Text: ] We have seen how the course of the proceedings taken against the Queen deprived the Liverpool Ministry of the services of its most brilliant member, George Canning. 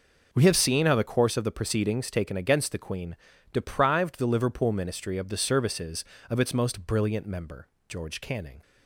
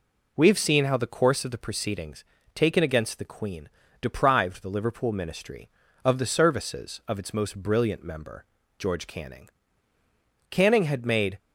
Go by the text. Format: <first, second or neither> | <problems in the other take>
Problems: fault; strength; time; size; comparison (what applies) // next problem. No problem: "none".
first | pauses between "proceedings" and "taken"; slight; at 2.2 s; 0.30 s long // pauses between "Queen" and "deprived"; slight; at 3.6 s; 0.32 s long; slight in the first // goes on to say "Canning had made"; noticeable; from 10.4 s on; 0.88 s long